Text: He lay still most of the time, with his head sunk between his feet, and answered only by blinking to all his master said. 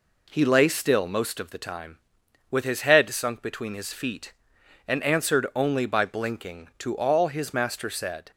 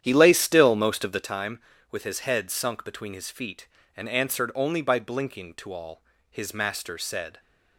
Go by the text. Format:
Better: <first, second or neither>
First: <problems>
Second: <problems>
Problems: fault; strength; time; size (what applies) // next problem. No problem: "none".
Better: first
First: none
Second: starts louder than the rest; strong; until 1.4 s; 10 dB // pauses between "all" and "his"; slight; at 6.0 s; 0.30 s long